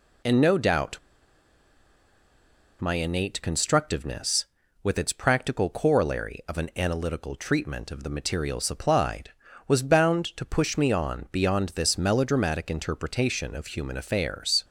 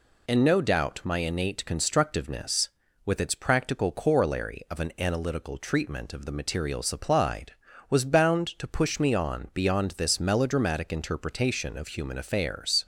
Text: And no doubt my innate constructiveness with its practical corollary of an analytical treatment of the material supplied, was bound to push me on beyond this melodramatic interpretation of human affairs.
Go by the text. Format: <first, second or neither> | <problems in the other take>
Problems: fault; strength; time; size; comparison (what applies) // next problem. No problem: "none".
second | pauses between "doubt" and "my"; strong; at 0.9 s; 1.8 s long